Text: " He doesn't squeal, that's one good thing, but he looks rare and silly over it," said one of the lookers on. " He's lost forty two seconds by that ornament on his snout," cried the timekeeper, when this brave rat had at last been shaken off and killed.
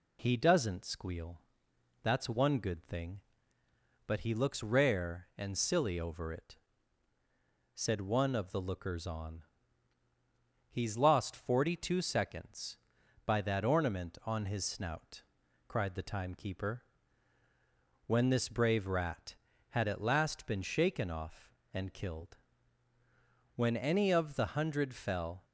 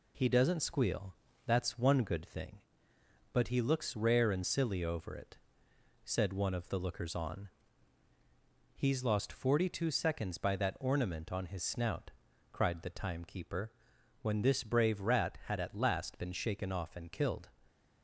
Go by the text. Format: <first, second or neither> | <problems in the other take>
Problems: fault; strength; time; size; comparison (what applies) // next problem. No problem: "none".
second | goes on to say "When any of the hundred fell"; strong; from 23.5 s on; 1.9 s long